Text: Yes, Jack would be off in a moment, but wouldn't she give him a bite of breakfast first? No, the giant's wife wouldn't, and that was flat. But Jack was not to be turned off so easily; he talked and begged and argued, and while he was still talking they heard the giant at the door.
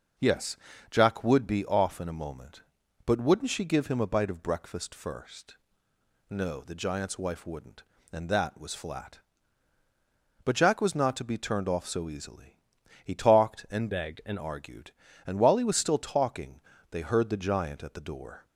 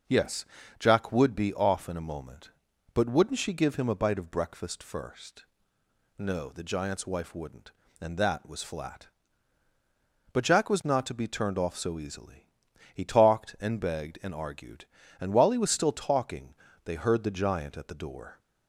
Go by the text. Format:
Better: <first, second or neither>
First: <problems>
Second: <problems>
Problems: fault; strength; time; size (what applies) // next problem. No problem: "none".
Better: second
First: changes voice from "begged" to "and"; from 13.9 to 14.3 s; 0.4 s long // pauses between "talking" and "they"; slight; at 16.6 s; 0.30 s long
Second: pauses between "talking" and "they"; slight; at 16.5 s; 0.30 s long